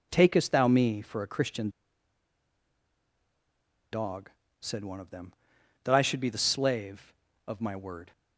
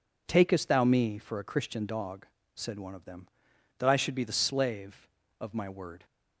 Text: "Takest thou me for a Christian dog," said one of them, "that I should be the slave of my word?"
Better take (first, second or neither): second